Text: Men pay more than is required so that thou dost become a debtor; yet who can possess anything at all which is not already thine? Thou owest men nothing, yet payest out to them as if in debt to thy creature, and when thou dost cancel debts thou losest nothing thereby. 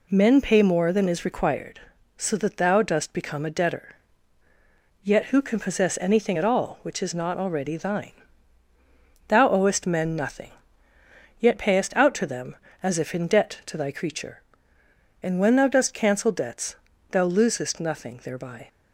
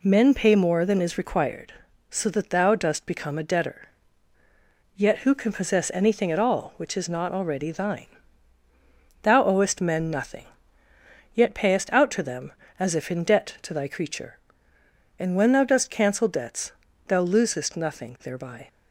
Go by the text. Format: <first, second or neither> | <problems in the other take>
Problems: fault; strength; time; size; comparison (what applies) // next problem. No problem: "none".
neither | pauses between "debts" and "thou"; slight; the same in both